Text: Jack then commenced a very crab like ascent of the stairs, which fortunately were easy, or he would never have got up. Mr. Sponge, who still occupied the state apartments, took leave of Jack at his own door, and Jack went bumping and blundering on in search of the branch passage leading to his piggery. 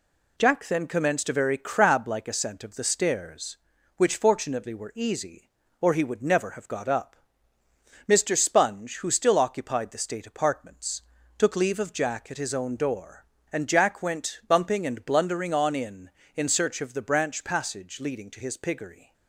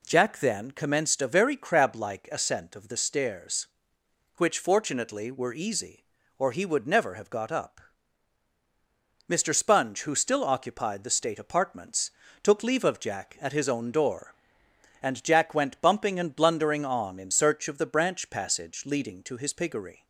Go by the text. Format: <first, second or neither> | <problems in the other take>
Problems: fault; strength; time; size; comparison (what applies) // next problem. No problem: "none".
second | says "in" twice; at 16.3 s